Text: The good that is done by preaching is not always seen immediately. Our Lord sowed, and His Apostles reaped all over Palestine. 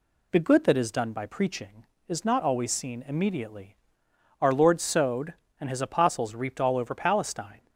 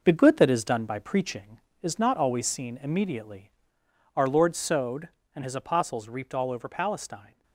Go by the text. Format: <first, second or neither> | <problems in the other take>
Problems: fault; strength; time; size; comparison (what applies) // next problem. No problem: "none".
first | gets quieter; strong; throughout; 7.5 dB